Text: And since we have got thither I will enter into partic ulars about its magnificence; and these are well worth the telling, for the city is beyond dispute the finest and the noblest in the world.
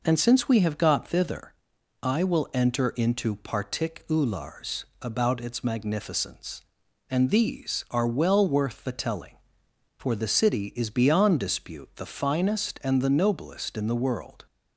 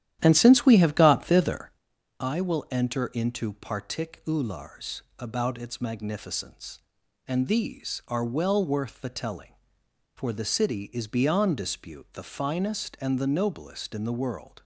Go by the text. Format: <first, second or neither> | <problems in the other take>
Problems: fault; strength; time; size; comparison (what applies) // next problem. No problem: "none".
first | starts louder than the rest; strong; until 1.8 s; 11.5 dB // pauses between "thither" and "I"; noticeable; at 1.7 s; 0.48 s long; noticeable in the first // pauses between "ulars" and "about"; slight; at 5.0 s; 0.16 s long; slight in the first